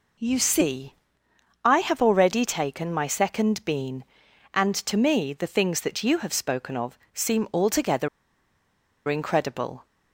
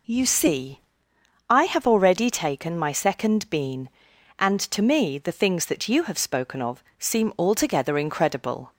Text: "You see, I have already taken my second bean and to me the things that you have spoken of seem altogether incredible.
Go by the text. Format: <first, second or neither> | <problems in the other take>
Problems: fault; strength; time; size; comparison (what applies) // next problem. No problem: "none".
second | pauses between "of" and "seem"; slight; at 6.9 s; 0.16 s long; slight in the second // pauses between "altogether" and "incredible"; at 8.0 s; 1.0 s long